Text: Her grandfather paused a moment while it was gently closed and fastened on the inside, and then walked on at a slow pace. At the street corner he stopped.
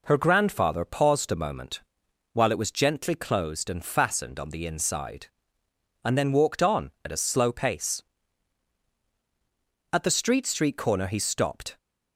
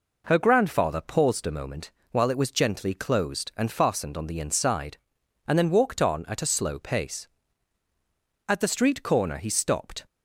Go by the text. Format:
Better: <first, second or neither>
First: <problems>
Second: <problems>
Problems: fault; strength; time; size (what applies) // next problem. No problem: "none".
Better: second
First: pauses between "moment" and "while"; noticeable; at 1.8 s; 0.52 s long // says "street" twice; at 10.4 s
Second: pauses between "moment" and "while"; slight; at 1.9 s; 0.20 s long